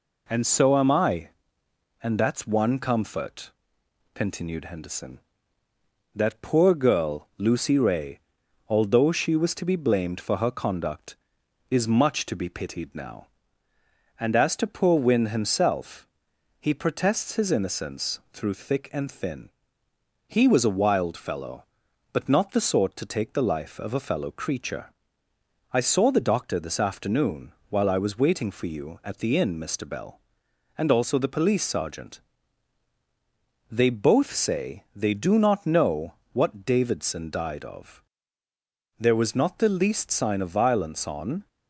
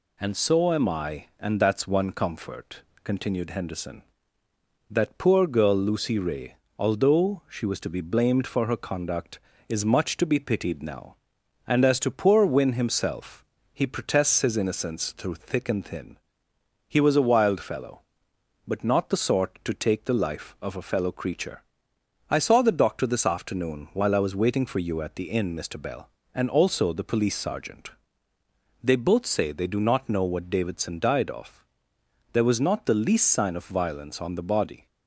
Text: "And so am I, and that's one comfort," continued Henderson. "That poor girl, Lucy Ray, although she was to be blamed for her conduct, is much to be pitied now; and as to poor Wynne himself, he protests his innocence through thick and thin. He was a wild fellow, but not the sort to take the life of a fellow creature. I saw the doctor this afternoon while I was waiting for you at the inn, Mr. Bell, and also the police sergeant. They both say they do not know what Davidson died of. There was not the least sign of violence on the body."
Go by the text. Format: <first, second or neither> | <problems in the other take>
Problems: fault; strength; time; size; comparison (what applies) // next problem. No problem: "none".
second | pauses between "afternoon" and "while"; slight; at 27.5 s; 0.16 s long // pauses between "know" and "what"; slight; at 36.1 s; 0.18 s long // stops before "the body"; at 41.4 s